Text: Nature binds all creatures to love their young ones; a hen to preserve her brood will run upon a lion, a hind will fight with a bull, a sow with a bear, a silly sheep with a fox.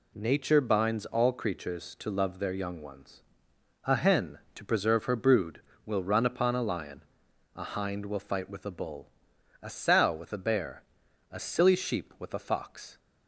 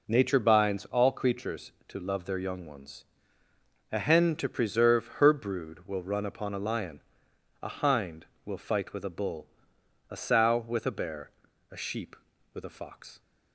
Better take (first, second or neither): first